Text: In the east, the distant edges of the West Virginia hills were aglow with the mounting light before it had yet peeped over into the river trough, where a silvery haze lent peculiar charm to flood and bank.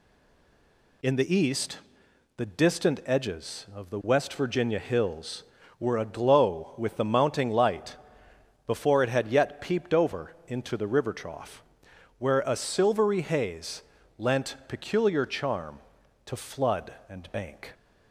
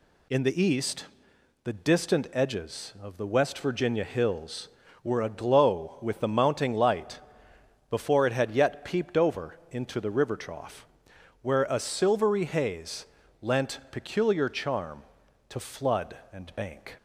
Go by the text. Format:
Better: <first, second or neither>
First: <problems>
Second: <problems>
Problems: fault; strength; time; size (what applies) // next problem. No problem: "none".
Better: second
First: stays silent before the first word; until 1.0 s; 1.0 s long // pauses between "light" and "before"; noticeable; at 7.9 s; 0.72 s long // pauses between "haze" and "lent"; slight; at 13.8 s; 0.36 s long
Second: pauses between "light" and "before"; noticeable; at 7.1 s; 0.72 s long // pauses between "haze" and "lent"; slight; at 13.0 s; 0.36 s long